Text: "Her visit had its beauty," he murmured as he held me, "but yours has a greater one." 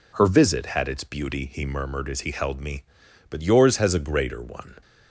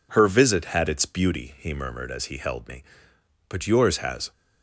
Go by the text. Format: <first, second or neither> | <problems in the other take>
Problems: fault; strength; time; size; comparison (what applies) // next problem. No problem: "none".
first | stops before "a greater one"; at 4.3 s